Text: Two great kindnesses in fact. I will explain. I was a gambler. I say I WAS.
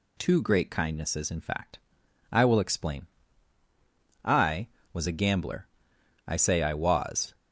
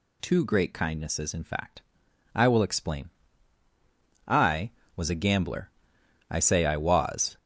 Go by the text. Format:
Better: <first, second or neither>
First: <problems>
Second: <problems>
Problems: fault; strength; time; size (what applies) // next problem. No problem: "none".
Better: first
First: none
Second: gets louder; throughout; 7 dB